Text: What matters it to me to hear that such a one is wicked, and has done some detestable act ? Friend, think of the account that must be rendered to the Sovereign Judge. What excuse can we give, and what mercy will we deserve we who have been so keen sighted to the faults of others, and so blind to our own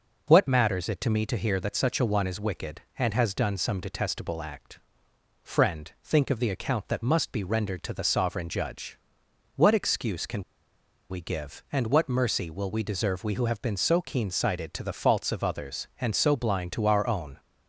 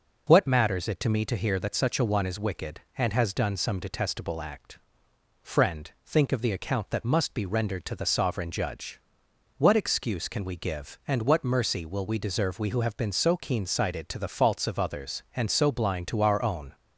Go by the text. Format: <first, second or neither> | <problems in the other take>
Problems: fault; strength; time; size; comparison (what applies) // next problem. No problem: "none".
second | pauses between "can" and "we"; noticeable; at 10.4 s; 0.67 s long